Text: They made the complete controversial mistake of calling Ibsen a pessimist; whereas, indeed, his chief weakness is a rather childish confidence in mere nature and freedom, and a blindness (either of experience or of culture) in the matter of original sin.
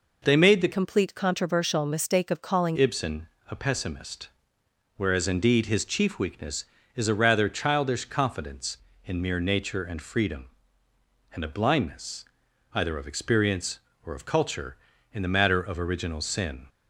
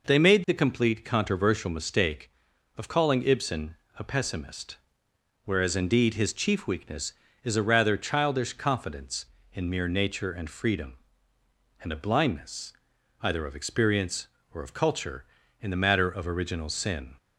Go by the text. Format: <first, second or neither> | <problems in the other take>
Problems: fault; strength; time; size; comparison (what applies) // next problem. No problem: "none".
second | changes voice from "complete" to "calling"; from 0.7 to 2.7 s; 2.0 s long // pauses between "Ibsen" and "a"; slight; at 3.2 s; 0.24 s long; slight in the second